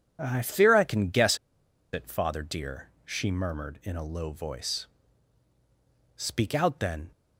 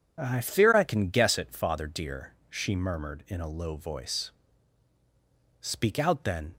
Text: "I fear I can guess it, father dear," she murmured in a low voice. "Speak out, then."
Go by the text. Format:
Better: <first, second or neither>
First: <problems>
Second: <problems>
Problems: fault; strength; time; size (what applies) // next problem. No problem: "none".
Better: second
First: pauses between "guess" and "it"; noticeable; at 1.3 s; 0.55 s long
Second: none